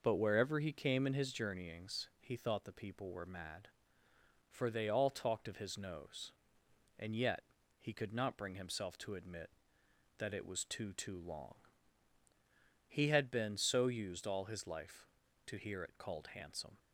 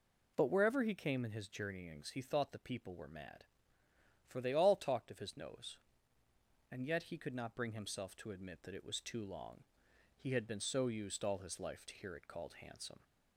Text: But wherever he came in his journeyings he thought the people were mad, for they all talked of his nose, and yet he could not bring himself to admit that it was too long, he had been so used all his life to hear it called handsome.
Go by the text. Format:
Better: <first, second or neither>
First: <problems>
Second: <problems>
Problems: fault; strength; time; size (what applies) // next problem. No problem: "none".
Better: second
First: pauses between "yet" and "he"; at 7.4 s; 0.40 s long // says "too" twice; at 10.9 s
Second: none